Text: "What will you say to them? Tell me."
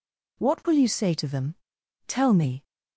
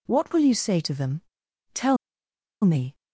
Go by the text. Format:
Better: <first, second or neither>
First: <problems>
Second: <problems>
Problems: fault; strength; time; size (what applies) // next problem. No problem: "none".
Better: first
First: none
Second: pauses between "Tell" and "me"; noticeable; at 1.9 s; 0.67 s long